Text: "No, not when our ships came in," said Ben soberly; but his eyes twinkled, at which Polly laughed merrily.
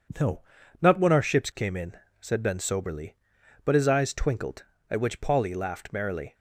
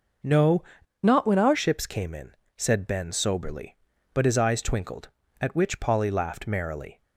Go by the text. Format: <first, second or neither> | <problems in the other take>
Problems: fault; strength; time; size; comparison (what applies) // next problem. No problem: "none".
first | changes voice from "not" to "our"; from 1.0 to 1.5 s; 0.5 s long